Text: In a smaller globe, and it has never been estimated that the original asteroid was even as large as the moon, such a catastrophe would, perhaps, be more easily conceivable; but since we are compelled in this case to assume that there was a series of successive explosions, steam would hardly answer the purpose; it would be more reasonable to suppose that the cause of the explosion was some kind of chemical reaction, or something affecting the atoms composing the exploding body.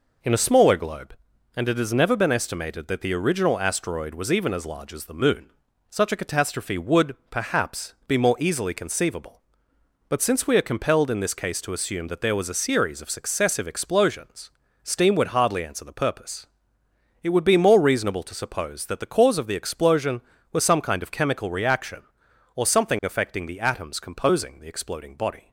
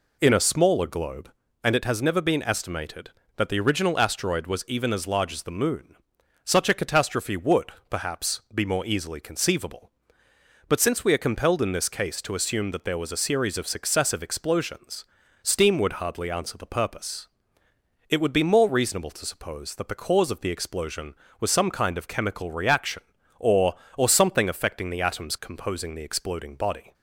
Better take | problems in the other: first | says "or" twice; at 23.9 s

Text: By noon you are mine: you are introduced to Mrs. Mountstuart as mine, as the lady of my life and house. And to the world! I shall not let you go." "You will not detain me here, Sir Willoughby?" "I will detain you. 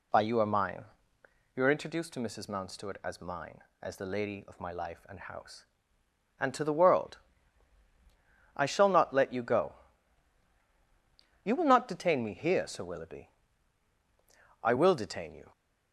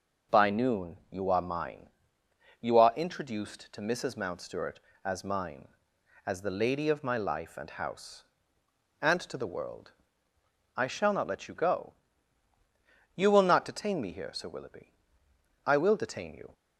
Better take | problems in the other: second | skips "noon"; at 0.2 s

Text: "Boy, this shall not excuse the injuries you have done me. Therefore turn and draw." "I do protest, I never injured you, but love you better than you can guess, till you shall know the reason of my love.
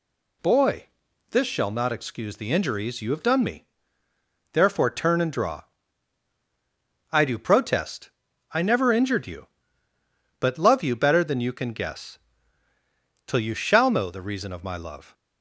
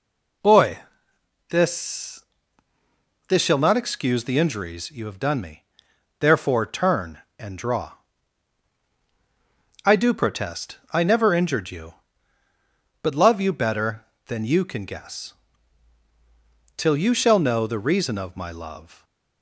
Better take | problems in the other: first | says "this" twice; at 3.2 s

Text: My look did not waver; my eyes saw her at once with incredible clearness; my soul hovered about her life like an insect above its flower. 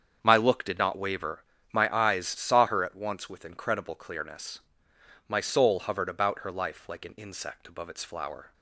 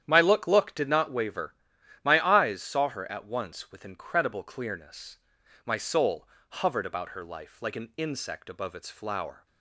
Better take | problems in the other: first | starts louder than the rest; strong; until 1.0 s; 10 dB; strong in the first // says "look" twice; at 0.4 s // pauses between "soul" and "hovered"; slight; at 6.2 s; 0.22 s long

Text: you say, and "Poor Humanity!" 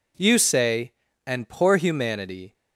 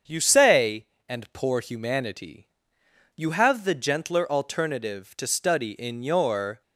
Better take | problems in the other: first | starts louder than the rest; strong; until 1.3 s; 7.5 dB // goes on to say "You have the gentler alternative to study in your"; strong; from 3.1 s on; 3.4 s long

